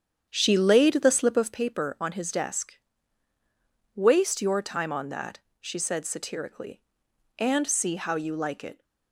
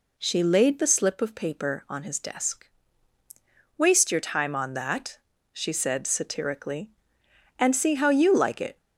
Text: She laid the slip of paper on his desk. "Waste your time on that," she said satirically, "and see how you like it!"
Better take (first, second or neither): second